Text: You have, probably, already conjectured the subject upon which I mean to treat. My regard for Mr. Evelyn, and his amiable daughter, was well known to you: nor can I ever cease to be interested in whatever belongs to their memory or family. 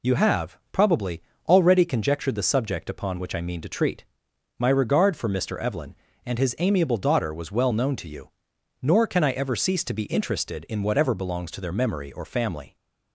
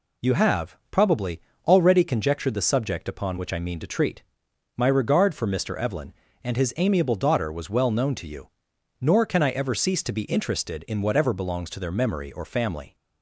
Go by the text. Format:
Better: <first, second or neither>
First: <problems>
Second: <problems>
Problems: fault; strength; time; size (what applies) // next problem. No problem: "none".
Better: neither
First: none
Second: none